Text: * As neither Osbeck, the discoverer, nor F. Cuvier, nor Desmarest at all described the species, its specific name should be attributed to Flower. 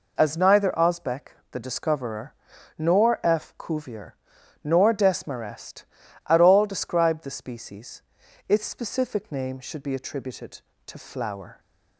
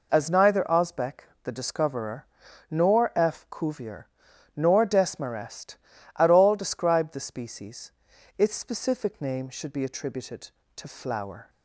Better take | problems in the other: neither | none

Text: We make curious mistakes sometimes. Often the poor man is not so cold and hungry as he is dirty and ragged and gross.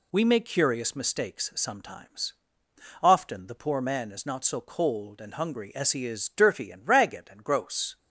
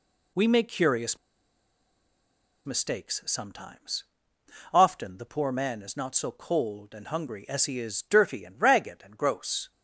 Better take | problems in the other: first | pauses between "curious" and "mistakes"; strong; at 1.1 s; 1.4 s long

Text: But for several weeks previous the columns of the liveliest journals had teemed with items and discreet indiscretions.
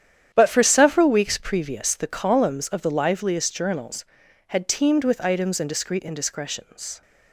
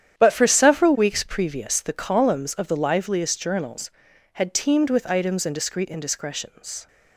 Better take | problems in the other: neither | starts louder than the rest; strong; the same in both

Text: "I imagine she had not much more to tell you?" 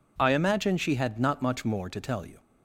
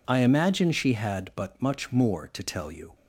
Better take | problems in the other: first | says "but" for "not"; at 1.3 s

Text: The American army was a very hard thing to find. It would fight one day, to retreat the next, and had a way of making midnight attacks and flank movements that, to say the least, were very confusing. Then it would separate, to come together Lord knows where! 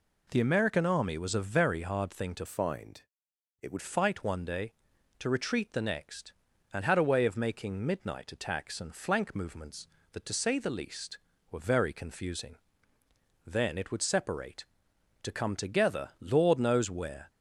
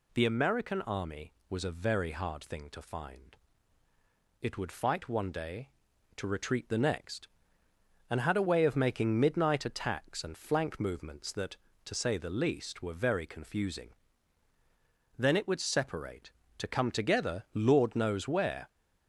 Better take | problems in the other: second | changes voice from "find" to "would"; from 2.4 to 3.7 s; 1.3 s long

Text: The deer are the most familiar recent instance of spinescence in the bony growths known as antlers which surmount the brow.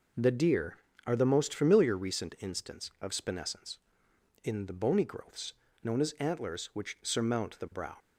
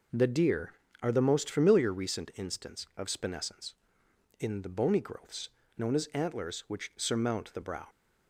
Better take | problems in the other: neither | pauses between "growths" and "known"; slight; the same in both

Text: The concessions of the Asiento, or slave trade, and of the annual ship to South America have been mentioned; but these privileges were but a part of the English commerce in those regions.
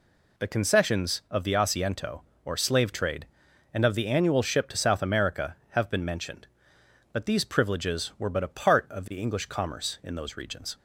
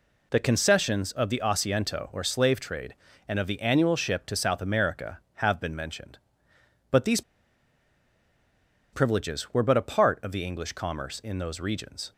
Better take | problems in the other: first | pauses between "these" and "privileges"; strong; at 7.2 s; 1.7 s long

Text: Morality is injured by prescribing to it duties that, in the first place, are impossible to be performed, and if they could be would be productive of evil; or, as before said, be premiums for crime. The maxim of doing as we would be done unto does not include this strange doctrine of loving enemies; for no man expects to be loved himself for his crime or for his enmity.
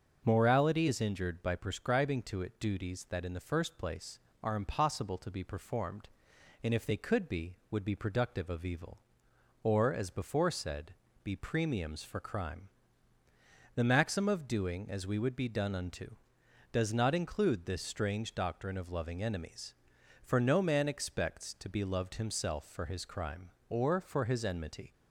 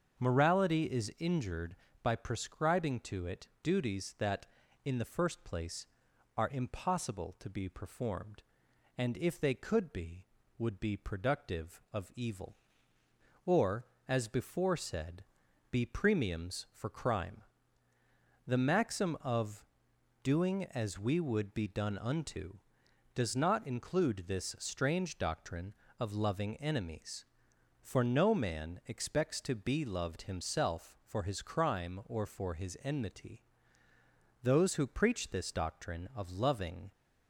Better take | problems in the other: first | starts louder than the rest; until 1.2 s; 7 dB; also in the first // pauses between "of" and "doing"; noticeable; at 19.6 s; 0.60 s long // goes on to say "Those who preach this doctrine of loving"; strong; from 34.4 s on; 2.4 s long

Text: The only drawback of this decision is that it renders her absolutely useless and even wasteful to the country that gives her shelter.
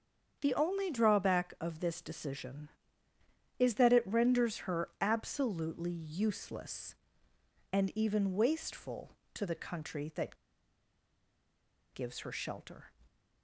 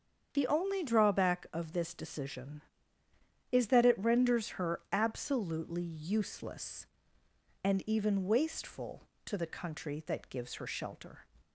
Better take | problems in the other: second | starts louder than the rest; strong; until 1.4 s; 7.5 dB; strong in the second // pauses between "that" and "gives"; strong; at 10.3 s; 1.5 s long

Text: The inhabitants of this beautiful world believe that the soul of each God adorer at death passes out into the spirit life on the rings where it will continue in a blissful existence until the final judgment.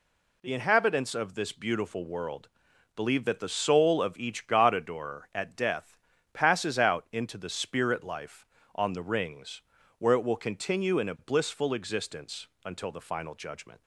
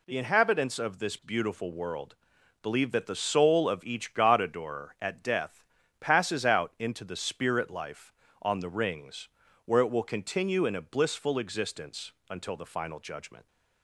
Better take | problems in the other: neither | pauses between "world" and "believe"; noticeable; the same in both // pauses between "death" and "passes"; slight; the same in both // pauses between "rings" and "where"; slight; the same in both // pauses between "existence" and "until"; slight; the same in both

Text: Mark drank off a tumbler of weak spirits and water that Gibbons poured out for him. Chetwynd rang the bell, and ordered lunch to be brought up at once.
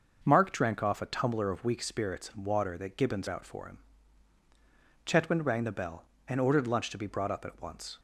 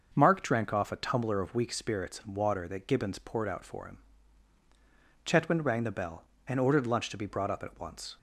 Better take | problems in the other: second | starts louder than the rest; noticeable; until 1.2 s; 6 dB; also in the second // skips "poured"; at 3.2 s

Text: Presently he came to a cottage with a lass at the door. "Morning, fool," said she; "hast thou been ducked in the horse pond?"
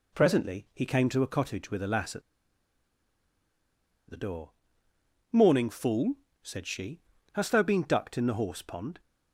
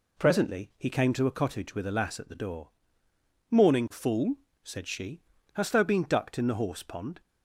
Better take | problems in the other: second | pauses between "at" and "the"; strong; at 2.2 s; 1.8 s long

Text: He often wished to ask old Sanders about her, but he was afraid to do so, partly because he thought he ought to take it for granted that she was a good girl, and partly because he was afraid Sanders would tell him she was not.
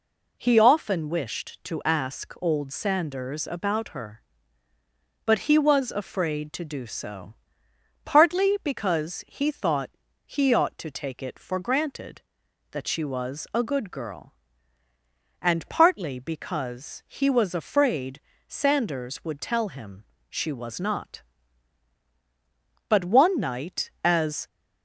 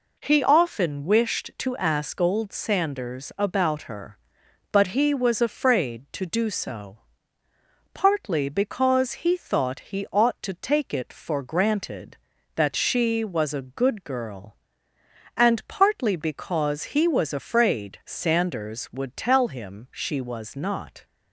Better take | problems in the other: second | pauses between "thought" and "he"; slight; at 9.9 s; 0.34 s long // pauses between "afraid" and "Sanders"; slight; at 18.2 s; 0.26 s long // pauses between "him" and "she"; slight; at 20.0 s; 0.26 s long // goes on to say "But one night as"; from 22.9 s on; 1.5 s long

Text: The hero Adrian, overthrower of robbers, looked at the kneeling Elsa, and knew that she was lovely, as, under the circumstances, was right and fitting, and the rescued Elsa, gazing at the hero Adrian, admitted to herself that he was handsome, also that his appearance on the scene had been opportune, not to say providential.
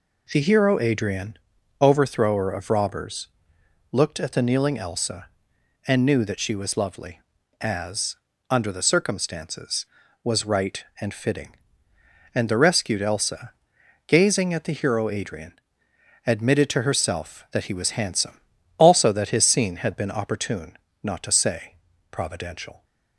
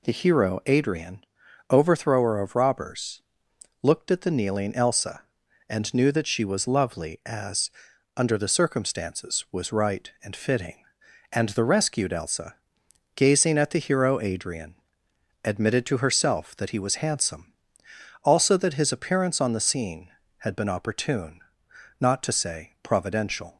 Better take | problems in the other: second | skips "appearance on the"; at 19.4 s // pauses between "say" and "providential"; slight; at 21.7 s; 0.36 s long

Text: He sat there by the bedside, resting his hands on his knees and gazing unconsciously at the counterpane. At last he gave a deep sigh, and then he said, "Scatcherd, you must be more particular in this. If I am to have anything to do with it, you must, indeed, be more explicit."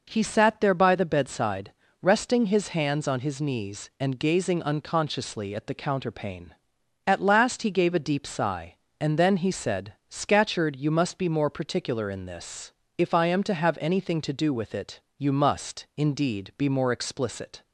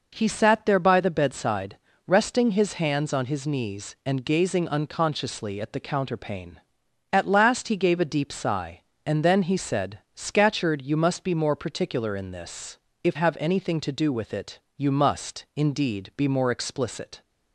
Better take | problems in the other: first | skips "I am to"; at 13.1 s

